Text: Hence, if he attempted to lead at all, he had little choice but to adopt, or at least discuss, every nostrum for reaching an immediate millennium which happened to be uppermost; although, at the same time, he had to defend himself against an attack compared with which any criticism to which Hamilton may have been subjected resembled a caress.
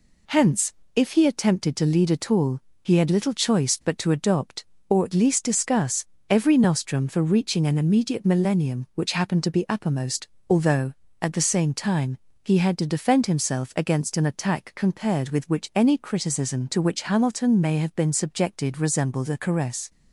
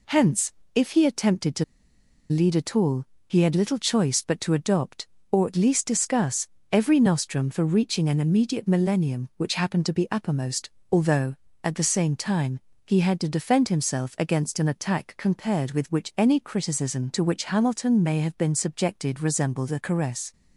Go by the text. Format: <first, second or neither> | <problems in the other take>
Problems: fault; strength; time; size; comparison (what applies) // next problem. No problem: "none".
first | pauses between "to" and "lead"; noticeable; at 1.6 s; 0.65 s long